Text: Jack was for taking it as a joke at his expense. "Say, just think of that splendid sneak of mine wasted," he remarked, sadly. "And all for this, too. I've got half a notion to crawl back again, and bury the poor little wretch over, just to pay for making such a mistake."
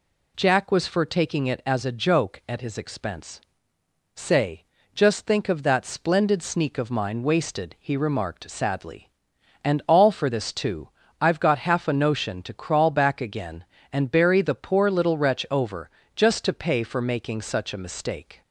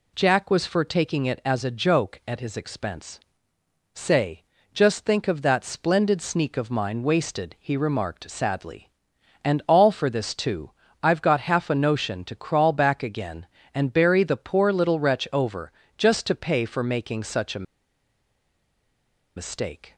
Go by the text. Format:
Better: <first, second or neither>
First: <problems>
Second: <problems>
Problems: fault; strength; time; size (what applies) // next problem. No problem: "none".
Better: first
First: none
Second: pauses between "a" and "mistake"; strong; at 17.6 s; 1.7 s long